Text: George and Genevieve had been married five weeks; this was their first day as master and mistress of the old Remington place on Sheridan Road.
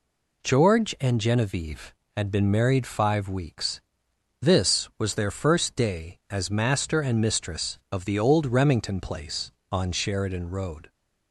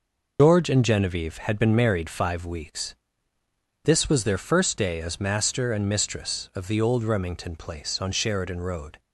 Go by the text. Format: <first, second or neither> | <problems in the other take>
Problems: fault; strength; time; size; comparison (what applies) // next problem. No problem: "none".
first | loses the start of "George"; at 0.3 s; 155 ms